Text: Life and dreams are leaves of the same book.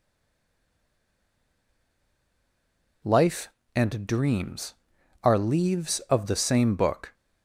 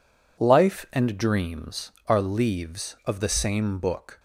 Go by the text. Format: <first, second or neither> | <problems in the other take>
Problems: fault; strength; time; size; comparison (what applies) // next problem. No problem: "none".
second | stays silent before the first word; strong; until 3.0 s; 3.0 s long